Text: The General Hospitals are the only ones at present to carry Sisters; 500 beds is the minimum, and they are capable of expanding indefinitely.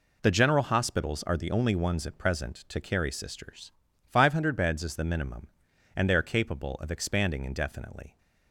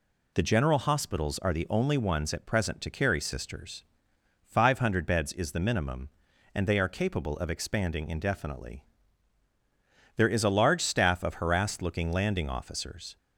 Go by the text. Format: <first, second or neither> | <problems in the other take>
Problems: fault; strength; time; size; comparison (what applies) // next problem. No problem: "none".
first | goes on to say "There is a large staff of harassed looking landing officers"; strong; from 10.1 s on; 3.0 s long